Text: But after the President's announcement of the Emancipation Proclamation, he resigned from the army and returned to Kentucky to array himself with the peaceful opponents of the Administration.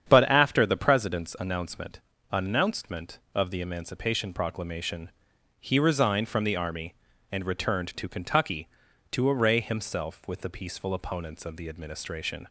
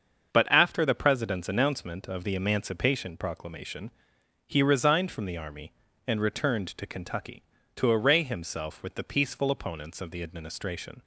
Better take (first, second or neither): second